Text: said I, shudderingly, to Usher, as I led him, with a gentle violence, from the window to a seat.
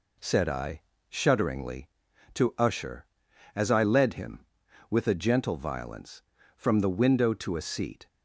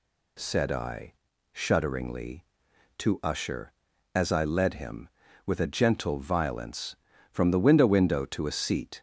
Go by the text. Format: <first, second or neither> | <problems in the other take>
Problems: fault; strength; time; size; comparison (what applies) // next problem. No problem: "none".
first | says "window" twice; at 7.8 s